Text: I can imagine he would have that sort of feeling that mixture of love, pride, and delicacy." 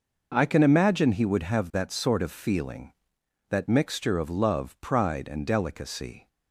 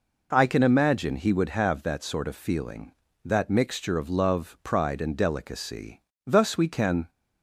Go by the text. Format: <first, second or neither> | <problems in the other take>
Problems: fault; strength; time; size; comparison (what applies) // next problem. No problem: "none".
first | goes on to say "Thus we can"; noticeable; from 6.2 s on; 0.84 s long